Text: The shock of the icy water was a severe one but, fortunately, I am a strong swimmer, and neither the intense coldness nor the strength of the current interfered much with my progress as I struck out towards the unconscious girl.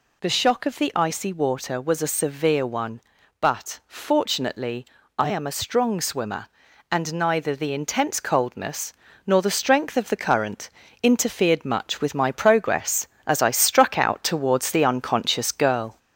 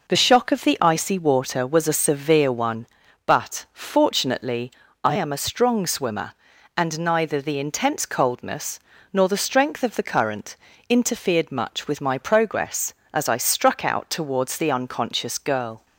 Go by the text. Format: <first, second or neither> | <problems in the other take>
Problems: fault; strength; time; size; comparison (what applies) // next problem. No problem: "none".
second | gets louder; slight; throughout; 2.5 dB // pauses between "coldness" and "nor"; slight; at 8.9 s; 0.34 s long; slight in the second // pauses between "current" and "interfered"; slight; at 10.7 s; 0.32 s long; slight in the second